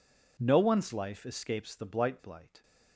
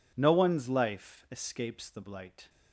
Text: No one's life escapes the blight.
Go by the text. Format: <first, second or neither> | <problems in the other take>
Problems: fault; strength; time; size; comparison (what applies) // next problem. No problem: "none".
second | says "blight" twice; at 2.2 s